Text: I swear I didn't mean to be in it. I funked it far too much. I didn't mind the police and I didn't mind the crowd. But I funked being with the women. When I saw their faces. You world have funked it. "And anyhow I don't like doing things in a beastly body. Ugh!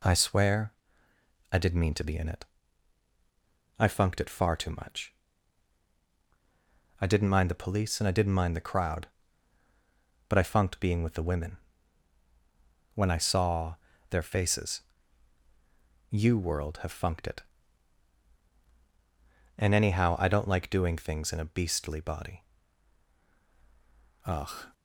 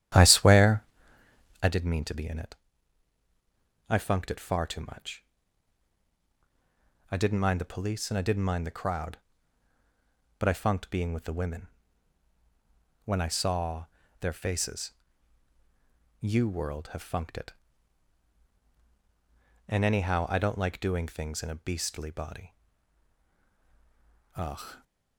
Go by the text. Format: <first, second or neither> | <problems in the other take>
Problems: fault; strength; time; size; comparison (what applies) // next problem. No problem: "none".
first | starts louder than the rest; strong; until 1.7 s; 11.5 dB // pauses between "swear" and "I"; noticeable; at 0.8 s; 0.80 s long; noticeable in the first // pauses between "saw" and "their"; slight; at 13.8 s; 0.34 s long; slight in the first